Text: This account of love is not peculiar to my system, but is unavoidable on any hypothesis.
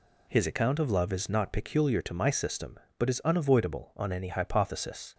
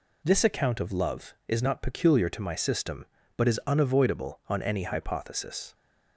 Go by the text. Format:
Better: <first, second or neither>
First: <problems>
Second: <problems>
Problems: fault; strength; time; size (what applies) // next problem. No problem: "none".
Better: second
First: says "His" for "This"; at 0.3 s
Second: none